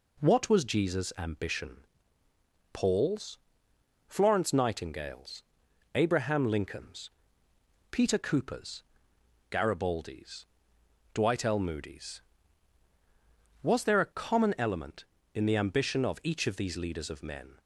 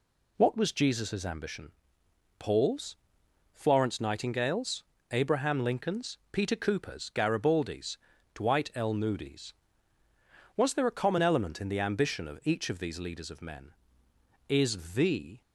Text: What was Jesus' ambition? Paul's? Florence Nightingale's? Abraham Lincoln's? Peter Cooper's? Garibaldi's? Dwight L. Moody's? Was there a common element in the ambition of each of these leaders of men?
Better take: first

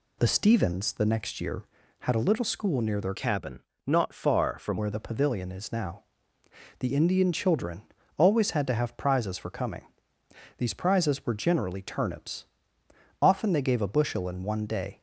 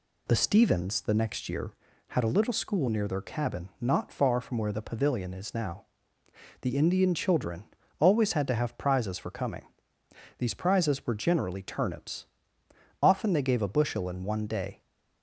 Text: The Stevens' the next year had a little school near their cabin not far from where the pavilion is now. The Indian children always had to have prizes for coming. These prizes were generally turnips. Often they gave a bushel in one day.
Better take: second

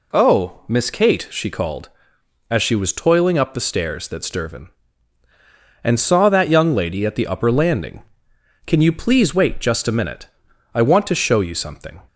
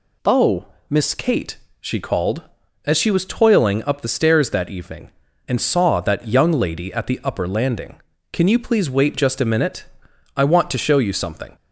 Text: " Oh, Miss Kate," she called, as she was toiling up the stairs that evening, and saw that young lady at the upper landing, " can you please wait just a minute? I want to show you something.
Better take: second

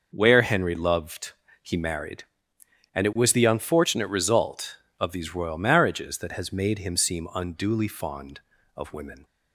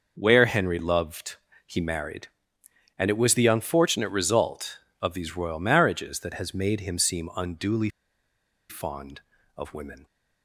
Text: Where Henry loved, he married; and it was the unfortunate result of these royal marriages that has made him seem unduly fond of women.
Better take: first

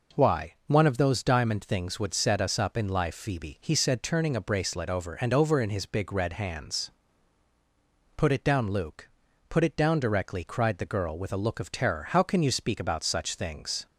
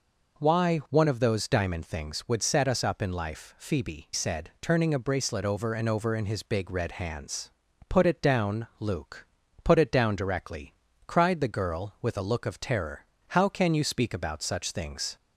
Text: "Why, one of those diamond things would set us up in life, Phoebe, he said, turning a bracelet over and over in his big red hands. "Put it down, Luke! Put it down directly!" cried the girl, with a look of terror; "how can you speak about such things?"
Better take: first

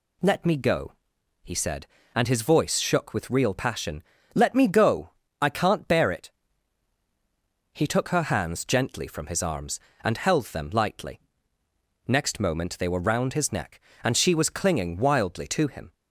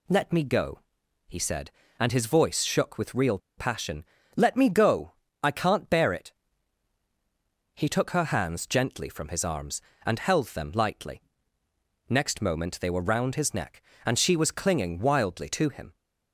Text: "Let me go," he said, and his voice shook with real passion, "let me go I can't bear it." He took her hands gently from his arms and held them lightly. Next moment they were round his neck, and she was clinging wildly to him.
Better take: first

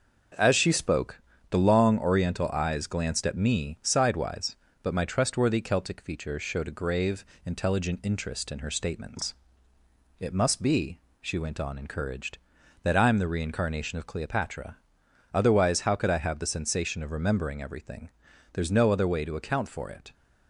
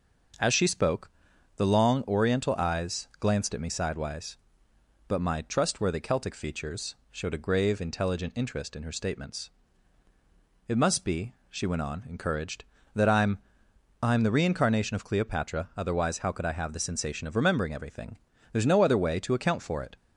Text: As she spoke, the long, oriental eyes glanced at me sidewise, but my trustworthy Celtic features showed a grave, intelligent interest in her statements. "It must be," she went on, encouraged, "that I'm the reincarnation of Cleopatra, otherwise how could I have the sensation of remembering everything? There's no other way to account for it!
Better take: first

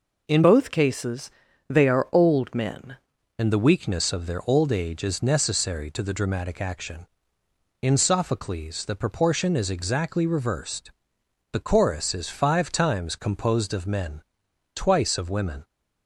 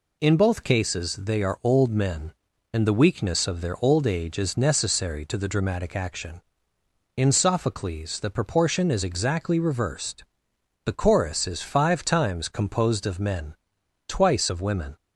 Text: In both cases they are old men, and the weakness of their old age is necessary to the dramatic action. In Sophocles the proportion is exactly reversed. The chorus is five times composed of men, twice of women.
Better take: second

